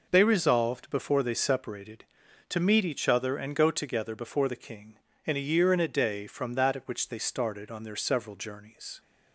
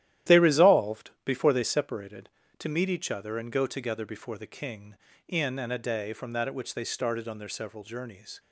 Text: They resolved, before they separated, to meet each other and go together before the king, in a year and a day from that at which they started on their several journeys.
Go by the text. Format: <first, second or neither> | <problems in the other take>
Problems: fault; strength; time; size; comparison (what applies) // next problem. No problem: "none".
first | starts louder than the rest; strong; until 1.4 s; 12 dB // skips "a year"; at 5.5 s